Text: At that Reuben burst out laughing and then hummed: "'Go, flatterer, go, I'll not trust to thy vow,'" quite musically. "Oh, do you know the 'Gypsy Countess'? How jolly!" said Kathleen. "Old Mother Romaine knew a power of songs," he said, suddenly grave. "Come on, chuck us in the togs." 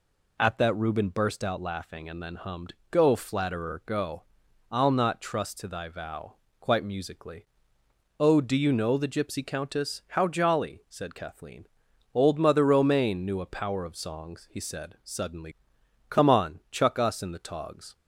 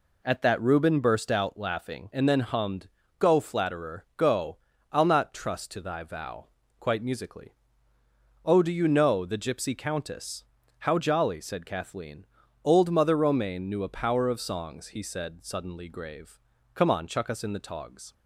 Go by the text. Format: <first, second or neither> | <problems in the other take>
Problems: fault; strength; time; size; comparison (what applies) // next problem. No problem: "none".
second | skips "grave"; at 15.8 s